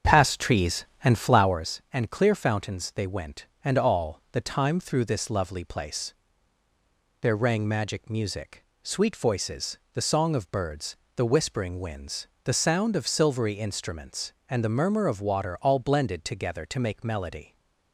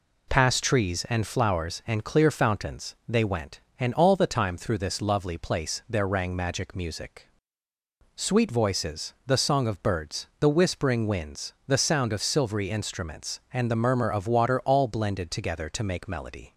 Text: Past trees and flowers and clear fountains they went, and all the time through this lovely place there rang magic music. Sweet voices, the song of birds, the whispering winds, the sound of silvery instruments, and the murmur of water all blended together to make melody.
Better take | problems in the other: second | starts louder than the rest; strong; until 1.7 s; 7.5 dB // pauses between "place" and "there"; at 6.1 s; 1.0 s long

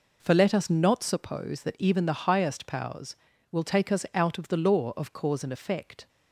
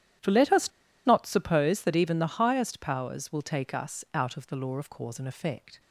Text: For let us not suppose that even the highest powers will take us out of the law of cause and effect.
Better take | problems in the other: first | starts louder than the rest; strong; until 1.5 s; 11.5 dB // pauses between "us" and "not"; at 0.6 s; 0.36 s long

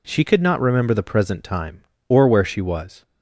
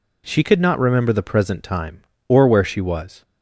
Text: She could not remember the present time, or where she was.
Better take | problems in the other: neither | none

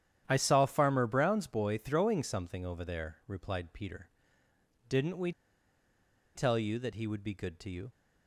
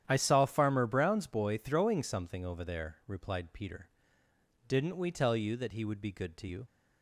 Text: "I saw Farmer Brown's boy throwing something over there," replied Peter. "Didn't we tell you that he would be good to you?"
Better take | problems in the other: second | starts louder than the rest; strong; until 1.2 s; 10 dB; strong in the second // pauses between "we" and "tell"; at 5.3 s; 1.0 s long

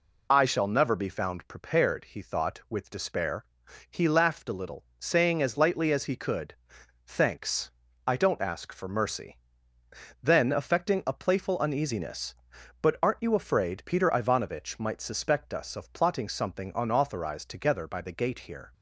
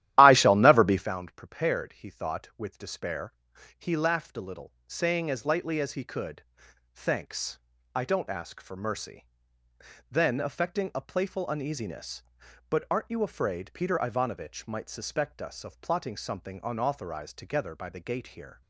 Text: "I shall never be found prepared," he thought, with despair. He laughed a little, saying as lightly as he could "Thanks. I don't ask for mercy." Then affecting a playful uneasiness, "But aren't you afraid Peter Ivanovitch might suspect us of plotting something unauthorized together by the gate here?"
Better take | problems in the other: first | starts louder than the rest; strong; until 1.1 s; 13.5 dB // pauses between "could" and "Thanks"; noticeable; at 6.4 s; 0.50 s long; noticeable in the first

